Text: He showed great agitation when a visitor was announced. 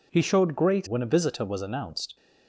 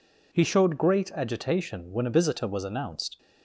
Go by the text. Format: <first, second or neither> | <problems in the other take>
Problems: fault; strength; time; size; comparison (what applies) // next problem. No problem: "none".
second | skips "agitation"; at 0.8 s